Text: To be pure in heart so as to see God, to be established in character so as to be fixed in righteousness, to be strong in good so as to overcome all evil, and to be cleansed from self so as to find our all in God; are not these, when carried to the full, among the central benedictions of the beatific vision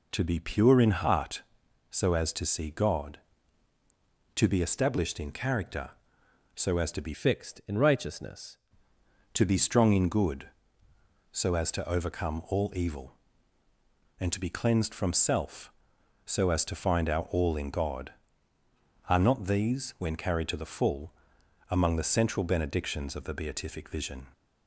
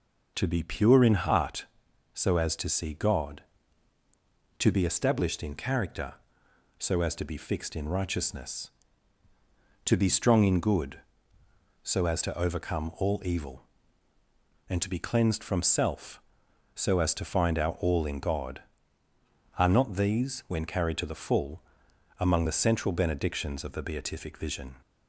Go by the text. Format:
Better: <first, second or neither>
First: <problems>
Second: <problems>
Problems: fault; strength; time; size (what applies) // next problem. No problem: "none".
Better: second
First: changes voice from "fixed" to "righteousness"; from 7.1 to 8.5 s; 1.4 s long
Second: none